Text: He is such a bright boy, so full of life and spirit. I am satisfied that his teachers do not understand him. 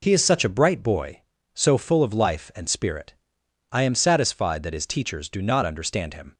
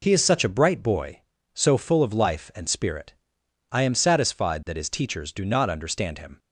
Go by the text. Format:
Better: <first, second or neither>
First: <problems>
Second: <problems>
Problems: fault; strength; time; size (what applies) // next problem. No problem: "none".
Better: neither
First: none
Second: none